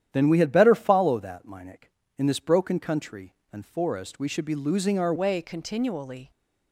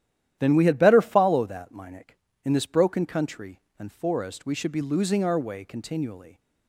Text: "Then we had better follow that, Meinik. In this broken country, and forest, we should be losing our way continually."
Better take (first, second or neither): second